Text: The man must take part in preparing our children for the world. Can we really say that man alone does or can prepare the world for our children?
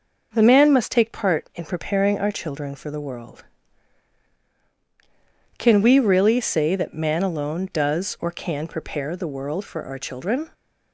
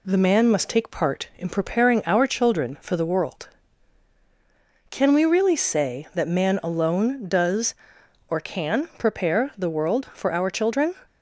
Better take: neither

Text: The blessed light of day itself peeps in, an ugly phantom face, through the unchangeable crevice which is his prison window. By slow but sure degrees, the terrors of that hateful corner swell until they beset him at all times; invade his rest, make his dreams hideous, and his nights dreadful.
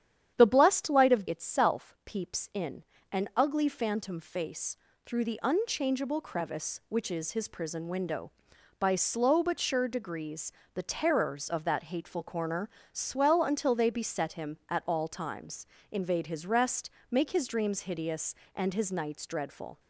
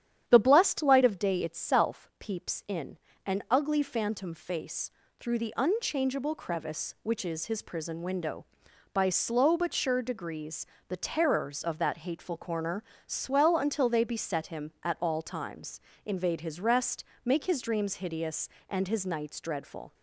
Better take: second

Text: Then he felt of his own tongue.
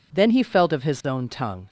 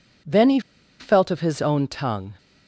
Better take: first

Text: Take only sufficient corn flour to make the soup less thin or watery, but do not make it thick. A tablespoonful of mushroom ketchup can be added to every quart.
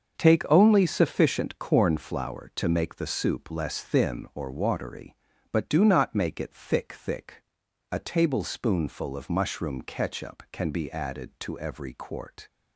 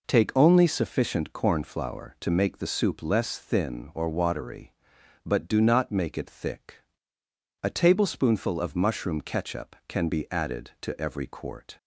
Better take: second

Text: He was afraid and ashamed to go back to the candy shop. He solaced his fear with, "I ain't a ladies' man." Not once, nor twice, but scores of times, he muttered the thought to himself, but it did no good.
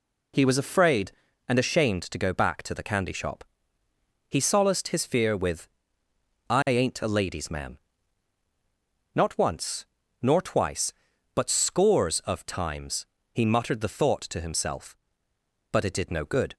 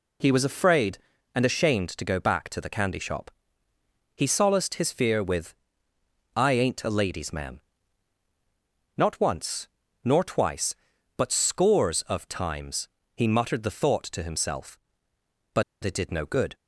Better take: first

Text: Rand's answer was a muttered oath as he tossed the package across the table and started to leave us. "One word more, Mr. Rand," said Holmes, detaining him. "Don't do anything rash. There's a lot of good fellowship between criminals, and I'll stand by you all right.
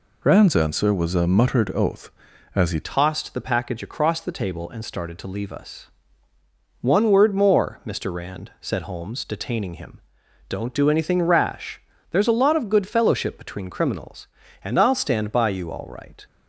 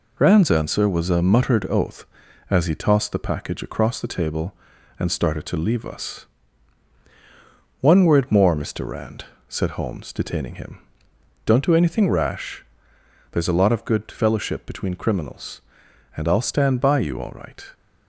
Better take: second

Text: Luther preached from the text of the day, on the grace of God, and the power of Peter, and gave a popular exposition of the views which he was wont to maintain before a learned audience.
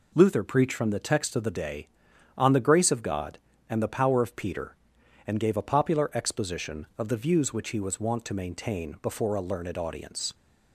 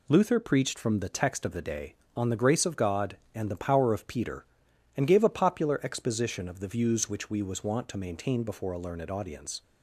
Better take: first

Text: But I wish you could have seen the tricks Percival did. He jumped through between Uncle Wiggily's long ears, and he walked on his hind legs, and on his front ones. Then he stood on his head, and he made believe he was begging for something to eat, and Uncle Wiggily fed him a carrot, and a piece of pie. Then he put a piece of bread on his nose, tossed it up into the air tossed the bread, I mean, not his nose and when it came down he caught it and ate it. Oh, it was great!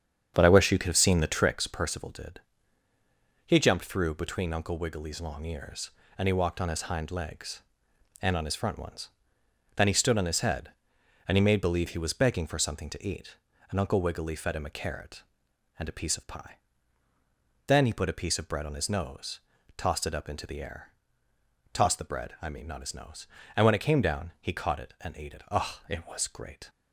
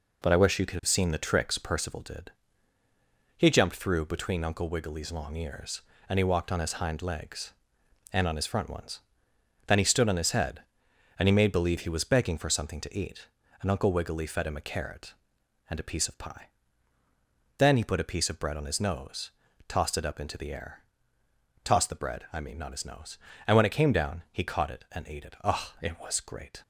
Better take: second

